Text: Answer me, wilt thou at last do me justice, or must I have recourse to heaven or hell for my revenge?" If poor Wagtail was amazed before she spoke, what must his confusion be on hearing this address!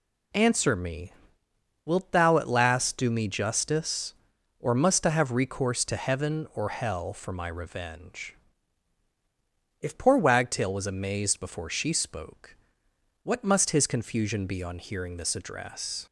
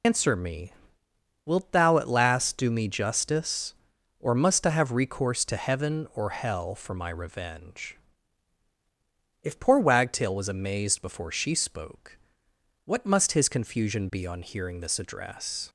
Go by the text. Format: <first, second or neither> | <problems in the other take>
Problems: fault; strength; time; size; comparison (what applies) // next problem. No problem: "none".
first | loses the start of "Answer"; at 0.0 s; 115 ms